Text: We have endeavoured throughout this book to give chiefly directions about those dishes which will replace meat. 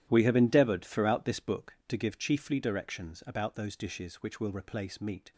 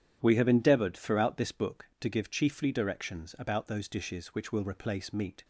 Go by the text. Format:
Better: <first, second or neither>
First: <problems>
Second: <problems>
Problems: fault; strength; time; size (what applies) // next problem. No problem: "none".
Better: second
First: gets quieter; strong; throughout; 15.5 dB // starts louder than the rest; strong; until 1.1 s; 12 dB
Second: starts louder than the rest; strong; until 1.2 s; 9.5 dB